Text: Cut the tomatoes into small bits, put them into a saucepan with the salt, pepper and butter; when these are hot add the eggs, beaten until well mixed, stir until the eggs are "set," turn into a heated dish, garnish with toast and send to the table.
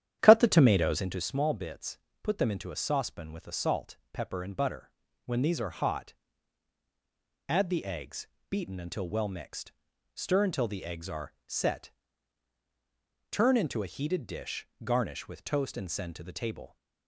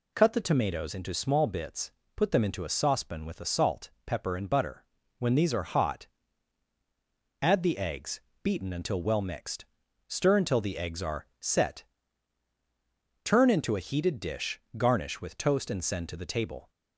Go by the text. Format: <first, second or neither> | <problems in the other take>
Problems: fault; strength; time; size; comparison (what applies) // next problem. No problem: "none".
second | starts louder than the rest; strong; until 1.3 s; 10.5 dB // pauses between "hot" and "add"; strong; at 6.1 s; 1.3 s long; strong in the second